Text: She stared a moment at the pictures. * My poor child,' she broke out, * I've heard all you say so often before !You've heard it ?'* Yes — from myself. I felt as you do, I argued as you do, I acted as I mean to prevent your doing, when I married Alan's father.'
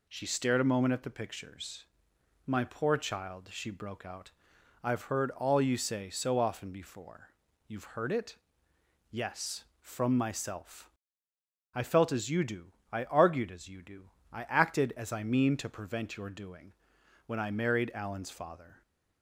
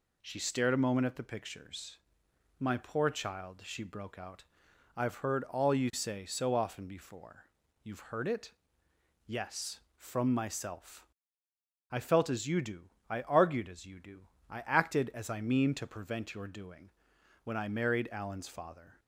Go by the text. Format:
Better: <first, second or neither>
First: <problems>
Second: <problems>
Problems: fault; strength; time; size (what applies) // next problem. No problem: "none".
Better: neither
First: none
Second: none